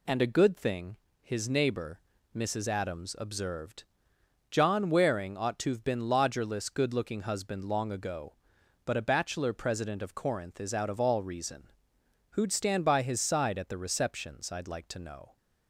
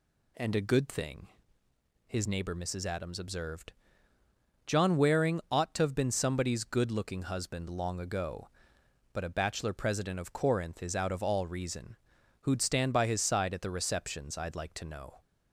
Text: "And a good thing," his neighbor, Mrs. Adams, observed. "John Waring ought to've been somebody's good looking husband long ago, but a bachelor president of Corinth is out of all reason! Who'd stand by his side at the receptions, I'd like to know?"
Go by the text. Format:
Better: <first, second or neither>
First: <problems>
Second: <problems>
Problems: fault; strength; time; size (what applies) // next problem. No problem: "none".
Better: second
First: says "lodgerless" for "somebody's"; at 6.0 s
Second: none